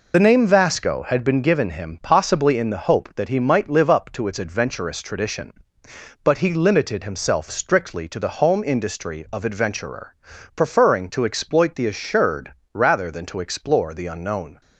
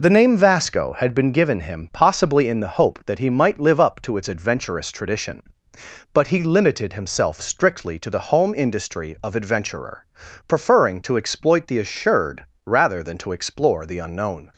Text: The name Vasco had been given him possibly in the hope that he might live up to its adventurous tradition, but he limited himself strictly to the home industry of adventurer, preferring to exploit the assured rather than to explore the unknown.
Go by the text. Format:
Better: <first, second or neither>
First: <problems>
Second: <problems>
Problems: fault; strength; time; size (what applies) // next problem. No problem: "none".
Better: second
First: loses the start of "The"; at 0.1 s; 45 ms // pauses between "assured" and "rather"; slight; at 12.5 s; 0.18 s long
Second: pauses between "assured" and "rather"; slight; at 12.4 s; 0.18 s long